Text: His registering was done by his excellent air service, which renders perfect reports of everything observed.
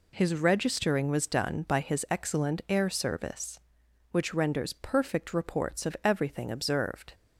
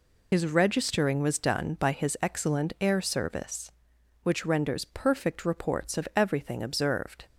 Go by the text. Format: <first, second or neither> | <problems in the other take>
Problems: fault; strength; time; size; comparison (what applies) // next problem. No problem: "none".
first | loses the start of "His"; at 0.3 s; 75 ms